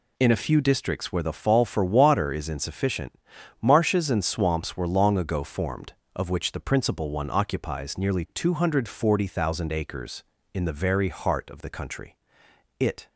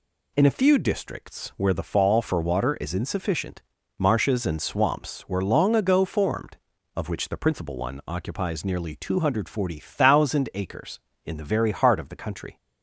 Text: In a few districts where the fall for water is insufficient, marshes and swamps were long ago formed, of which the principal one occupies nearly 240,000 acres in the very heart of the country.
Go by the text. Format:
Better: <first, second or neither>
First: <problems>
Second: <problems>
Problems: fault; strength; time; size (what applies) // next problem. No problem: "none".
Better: second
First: goes on to say "It"; slight; from 12.8 s on; 0.28 s long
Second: none